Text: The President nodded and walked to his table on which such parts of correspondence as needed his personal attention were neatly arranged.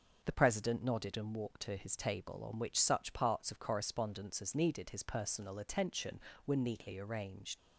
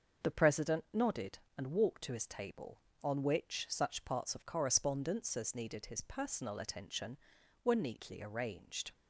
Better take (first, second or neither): second